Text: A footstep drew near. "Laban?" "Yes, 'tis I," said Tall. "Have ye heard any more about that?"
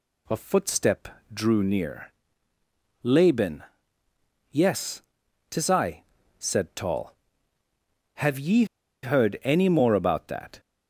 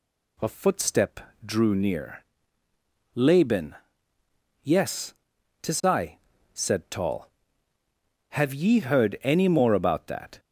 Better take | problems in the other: second | pauses between "footstep" and "drew"; slight; at 1.0 s; 0.24 s long; slight in the second // pauses between "ye" and "heard"; at 8.6 s; 0.38 s long

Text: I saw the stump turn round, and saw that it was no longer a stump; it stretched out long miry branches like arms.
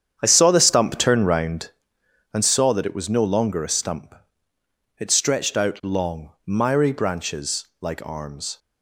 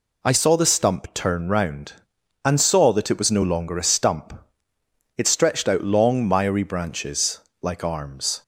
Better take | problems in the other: second | starts louder than the rest; strong; until 1.9 s; 8.5 dB // pauses between "branches" and "like"; slight; at 7.6 s; 0.16 s long; slight in the second

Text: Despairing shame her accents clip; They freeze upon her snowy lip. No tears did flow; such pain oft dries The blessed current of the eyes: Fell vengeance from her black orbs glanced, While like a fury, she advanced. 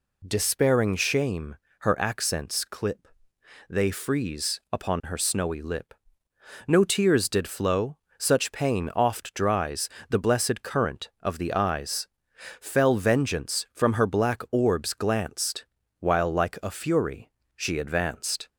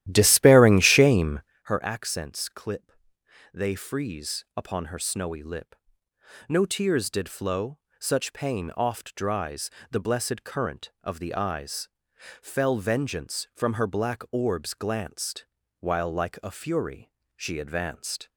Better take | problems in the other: first | starts louder than the rest; strong; until 1.6 s; 13 dB // pauses between "shame" and "her"; slight; at 1.4 s; 0.22 s long; slight in the first // pauses between "dries" and "The"; slight; at 9.6 s; 0.22 s long; slight in the first

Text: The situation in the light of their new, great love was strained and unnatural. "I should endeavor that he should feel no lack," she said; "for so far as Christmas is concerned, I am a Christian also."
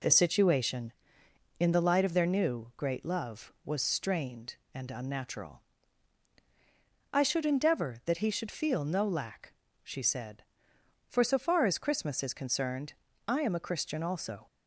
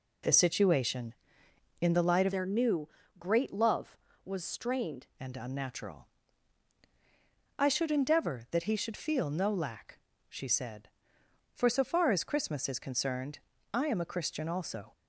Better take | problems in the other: first | changes voice from "their" to "strained"; from 2.3 to 5.0 s; 2.7 s long

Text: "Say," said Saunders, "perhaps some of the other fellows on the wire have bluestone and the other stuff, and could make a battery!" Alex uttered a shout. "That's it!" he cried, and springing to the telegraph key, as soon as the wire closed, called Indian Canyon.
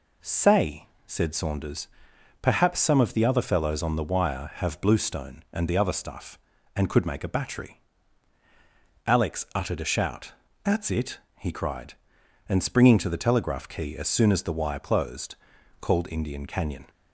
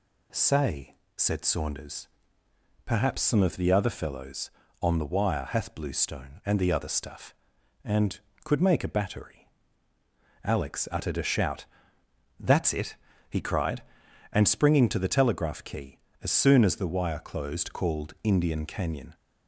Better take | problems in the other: first | says "hath" for "have"; at 5.4 s

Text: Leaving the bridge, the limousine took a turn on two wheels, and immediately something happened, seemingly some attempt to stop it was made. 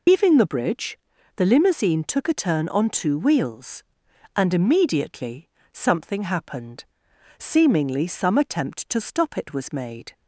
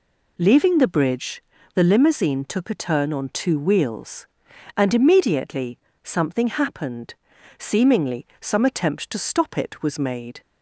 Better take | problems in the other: second | loses the start of "Leaving"; at 0.0 s; 130 ms // pauses between "immediately" and "something"; slight; at 5.4 s; 0.24 s long; slight in the second

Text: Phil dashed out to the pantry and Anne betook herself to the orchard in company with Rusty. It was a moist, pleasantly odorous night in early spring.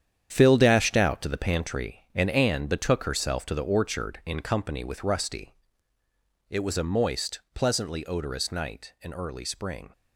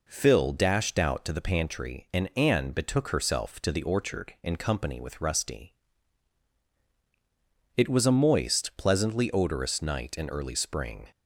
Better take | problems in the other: second | gets quieter; strong; throughout; 10 dB

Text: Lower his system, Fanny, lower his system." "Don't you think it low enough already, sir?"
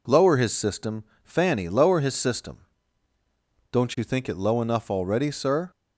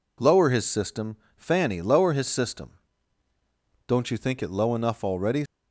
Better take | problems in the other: first | stops before "sir"; at 5.4 s

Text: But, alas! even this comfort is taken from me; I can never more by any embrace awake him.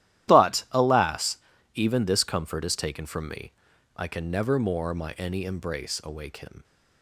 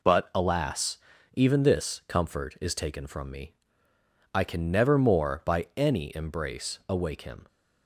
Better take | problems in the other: second | starts louder than the rest; strong; until 1.3 s; 13 dB // says "my" for "by"; at 4.9 s

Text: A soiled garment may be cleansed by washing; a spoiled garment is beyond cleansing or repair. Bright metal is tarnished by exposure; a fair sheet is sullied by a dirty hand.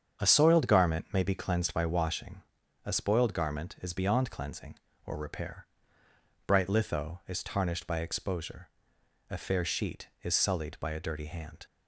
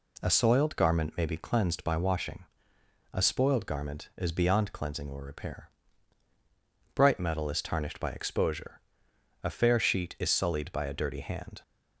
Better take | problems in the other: second | starts louder than the rest; strong; until 1.2 s; 7.5 dB // says "litho" for "metal"; at 6.6 s

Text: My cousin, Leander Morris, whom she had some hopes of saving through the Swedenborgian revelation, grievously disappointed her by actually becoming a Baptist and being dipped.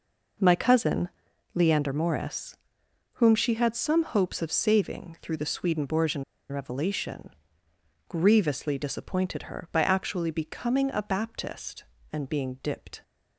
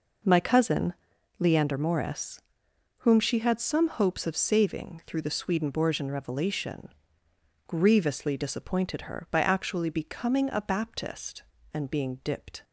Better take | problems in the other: second | pauses between "Swedenborgian" and "revelation"; slight; at 6.2 s; 0.26 s long

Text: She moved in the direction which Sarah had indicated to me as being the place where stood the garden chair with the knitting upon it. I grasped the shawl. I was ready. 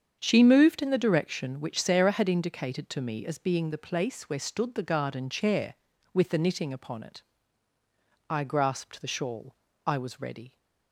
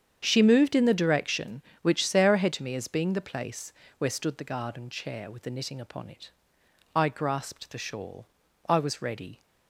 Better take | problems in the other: first | starts louder than the rest; strong; until 1.2 s; 8 dB; strong in the first // skips "indicated"; at 2.5 s // pauses between "place" and "where"; slight; at 3.7 s; 0.24 s long

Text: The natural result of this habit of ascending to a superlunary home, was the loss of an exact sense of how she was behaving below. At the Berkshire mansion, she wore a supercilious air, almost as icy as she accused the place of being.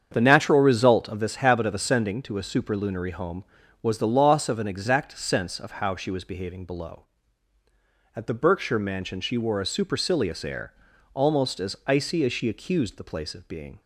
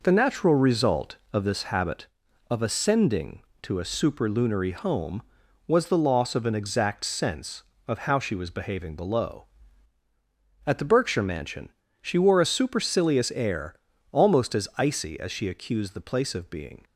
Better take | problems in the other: second | starts louder than the rest; strong; until 1.2 s; 7.5 dB

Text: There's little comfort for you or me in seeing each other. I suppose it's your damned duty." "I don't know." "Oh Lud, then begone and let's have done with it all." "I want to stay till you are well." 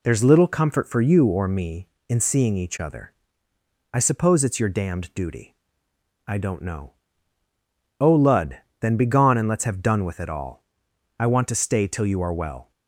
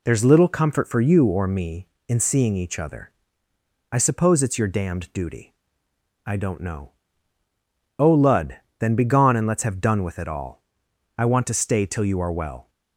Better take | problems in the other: neither | none

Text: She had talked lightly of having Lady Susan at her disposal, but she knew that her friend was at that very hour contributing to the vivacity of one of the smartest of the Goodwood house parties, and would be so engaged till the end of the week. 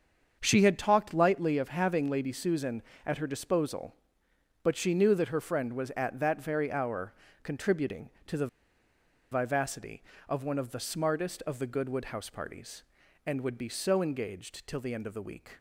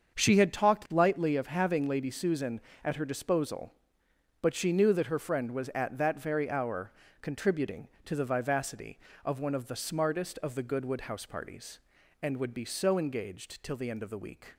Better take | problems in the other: second | starts louder than the rest; until 1.4 s; 7 dB; also in the second // pauses between "hour" and "contributing"; slight; at 7.1 s; 0.30 s long; slight in the second // pauses between "the" and "vivacity"; noticeable; at 8.4 s; 0.84 s long

